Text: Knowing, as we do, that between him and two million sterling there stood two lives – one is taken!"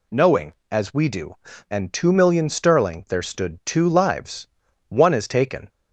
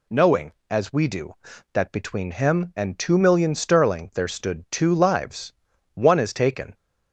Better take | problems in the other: second | skips "that between him"; at 1.5 s

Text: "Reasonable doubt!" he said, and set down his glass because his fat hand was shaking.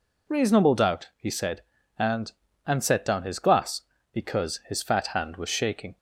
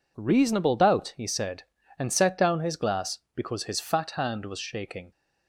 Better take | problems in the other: second | says "and" twice; at 2.6 s

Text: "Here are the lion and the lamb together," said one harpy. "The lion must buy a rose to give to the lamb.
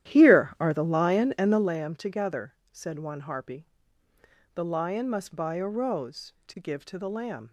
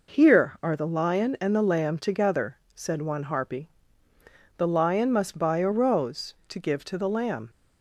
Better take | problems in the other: second | starts louder than the rest; strong; until 1.7 s; 12 dB

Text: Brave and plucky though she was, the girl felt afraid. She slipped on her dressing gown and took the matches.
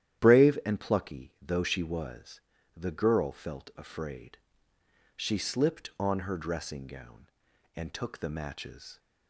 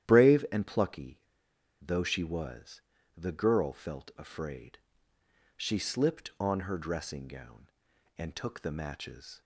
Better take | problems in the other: first | starts louder than the rest; strong; until 1.1 s; 11 dB; strong in the first // pauses between "plucky" and "though"; noticeable; at 1.1 s; 0.61 s long

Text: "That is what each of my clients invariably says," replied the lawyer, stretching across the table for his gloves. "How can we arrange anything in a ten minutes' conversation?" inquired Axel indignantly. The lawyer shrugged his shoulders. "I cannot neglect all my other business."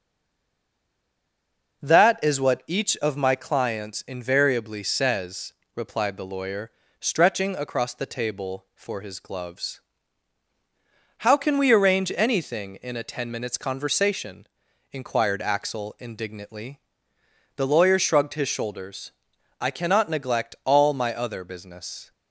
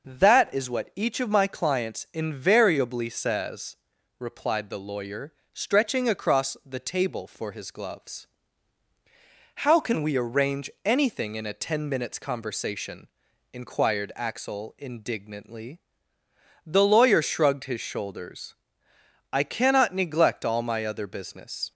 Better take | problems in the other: second | stays silent before the first word; noticeable; until 1.8 s; 1.8 s long

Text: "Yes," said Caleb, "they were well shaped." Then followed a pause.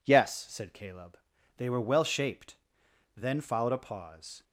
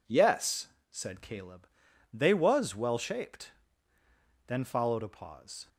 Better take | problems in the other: first | says "was" for "were"; at 2.3 s

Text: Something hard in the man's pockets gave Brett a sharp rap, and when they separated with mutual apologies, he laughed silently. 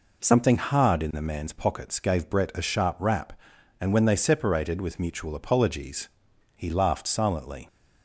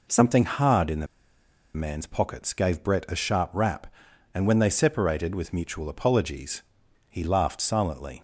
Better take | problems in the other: first | pauses between "the" and "man's"; noticeable; at 1.0 s; 0.68 s long

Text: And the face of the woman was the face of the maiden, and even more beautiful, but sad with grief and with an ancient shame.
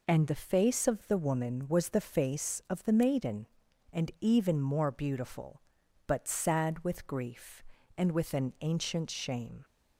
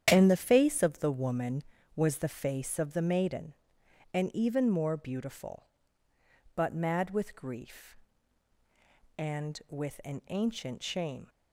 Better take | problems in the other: first | starts louder than the rest; strong; until 1.1 s; 9.5 dB // says "mad" for "sad"; at 6.7 s

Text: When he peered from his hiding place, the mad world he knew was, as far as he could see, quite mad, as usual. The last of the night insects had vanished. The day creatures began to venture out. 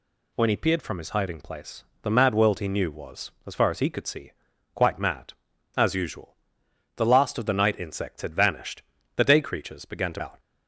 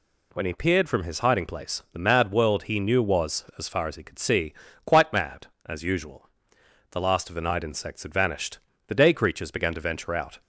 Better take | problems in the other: second | skips "venture"; at 10.2 s

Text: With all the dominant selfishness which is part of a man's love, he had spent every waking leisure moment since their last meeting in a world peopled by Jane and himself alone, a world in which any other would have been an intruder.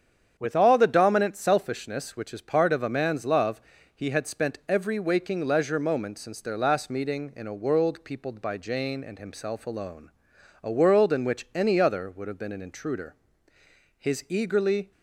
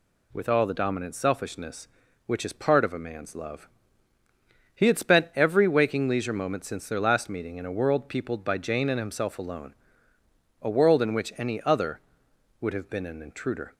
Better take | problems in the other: second | starts louder than the rest; strong; until 1.3 s; 8 dB // goes on to say "His eagerly"; noticeable; from 13.9 s on; 0.94 s long

